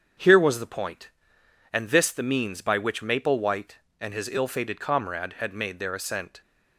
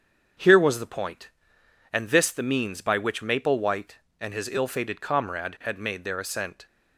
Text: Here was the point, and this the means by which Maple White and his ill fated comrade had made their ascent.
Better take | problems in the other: neither | starts louder than the rest; strong; the same in both

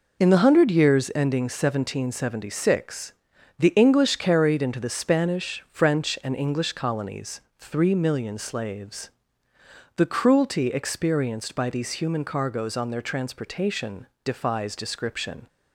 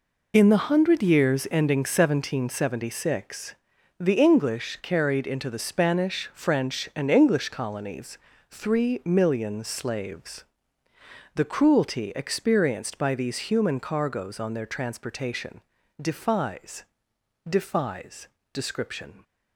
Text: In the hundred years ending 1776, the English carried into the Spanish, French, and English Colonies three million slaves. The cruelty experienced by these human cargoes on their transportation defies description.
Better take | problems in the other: first | pauses between "Colonies" and "three"; slight; at 8.1 s; 0.34 s long; slight in the first // pauses between "transportation" and "defies"; at 15.6 s; 0.40 s long; slight in the first // says "defies" twice; at 17.4 s

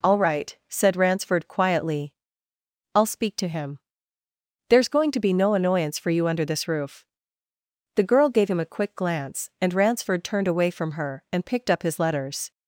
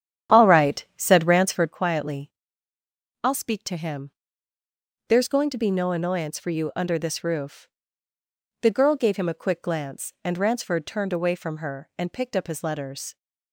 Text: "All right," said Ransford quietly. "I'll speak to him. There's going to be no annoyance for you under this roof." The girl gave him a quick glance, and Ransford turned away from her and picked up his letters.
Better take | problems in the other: first | starts louder than the rest; strong; until 1.8 s; 10 dB

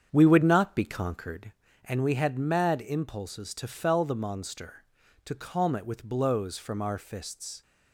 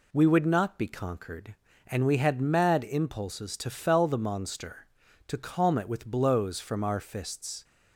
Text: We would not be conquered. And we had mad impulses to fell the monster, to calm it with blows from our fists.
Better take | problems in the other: second | starts louder than the rest; strong; until 1.6 s; 8 dB

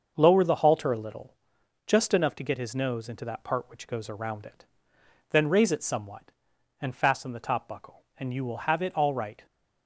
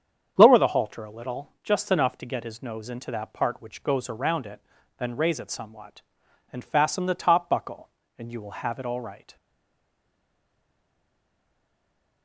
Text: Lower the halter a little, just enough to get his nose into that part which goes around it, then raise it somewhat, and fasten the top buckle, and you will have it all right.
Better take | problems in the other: first | starts louder than the rest; strong; until 1.3 s; 8 dB; also in the first // stays silent after the last word; strong; from 9.3 s on; 2.9 s long

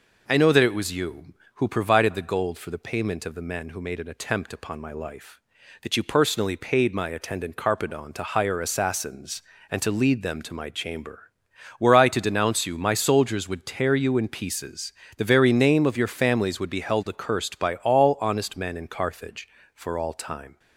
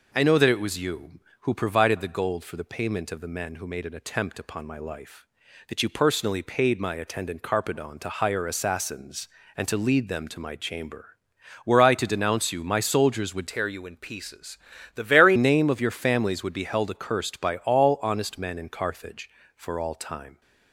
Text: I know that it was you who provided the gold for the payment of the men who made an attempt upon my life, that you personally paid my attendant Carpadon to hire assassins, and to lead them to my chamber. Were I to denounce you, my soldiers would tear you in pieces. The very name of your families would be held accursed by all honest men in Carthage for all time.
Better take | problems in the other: first | changes voice from "tear" to "very"; from 13.4 to 15.3 s; 1.9 s long

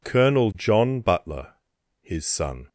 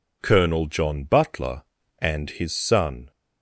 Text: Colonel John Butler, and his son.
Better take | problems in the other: second | skips "and"; at 1.7 s

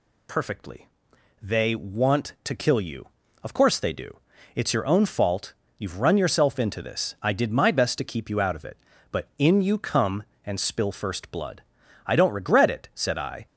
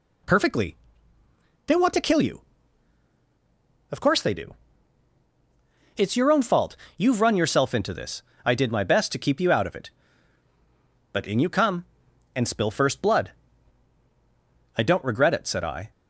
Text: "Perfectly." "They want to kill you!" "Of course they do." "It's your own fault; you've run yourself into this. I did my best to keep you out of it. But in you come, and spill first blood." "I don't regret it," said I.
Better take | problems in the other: neither | none

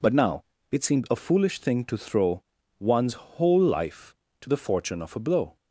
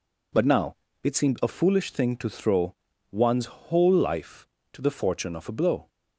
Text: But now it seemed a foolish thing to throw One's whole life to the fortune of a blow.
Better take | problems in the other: neither | pauses between "now" and "it"; slight; the same in both // pauses between "throw" and "One's"; the same in both

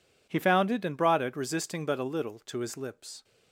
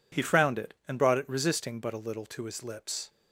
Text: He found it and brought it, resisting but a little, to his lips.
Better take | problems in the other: first | says "frowned" for "found"; at 0.2 s

